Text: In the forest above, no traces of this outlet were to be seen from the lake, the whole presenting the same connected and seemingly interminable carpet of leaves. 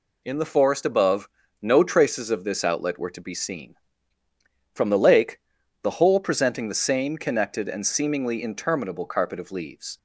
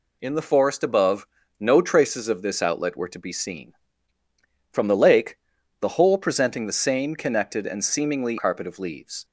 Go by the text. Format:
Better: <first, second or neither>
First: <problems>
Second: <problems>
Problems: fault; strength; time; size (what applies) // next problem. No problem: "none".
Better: first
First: none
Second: skips "interminable"; at 8.3 s